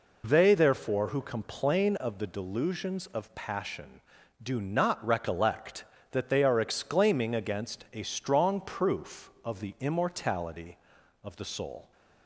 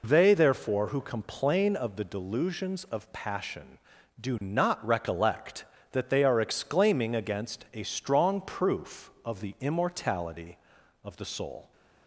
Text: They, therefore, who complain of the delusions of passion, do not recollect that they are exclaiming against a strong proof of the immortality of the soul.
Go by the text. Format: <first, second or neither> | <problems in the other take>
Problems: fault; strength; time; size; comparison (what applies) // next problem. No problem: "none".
neither | none